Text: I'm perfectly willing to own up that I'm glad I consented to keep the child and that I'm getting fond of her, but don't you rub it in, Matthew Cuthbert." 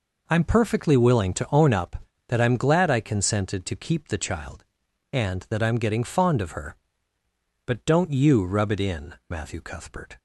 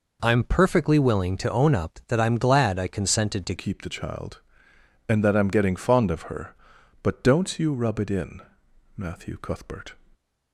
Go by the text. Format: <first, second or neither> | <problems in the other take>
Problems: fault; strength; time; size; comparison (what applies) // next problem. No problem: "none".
first | changes voice at "keep"; from 3.5 s on; 6.4 s long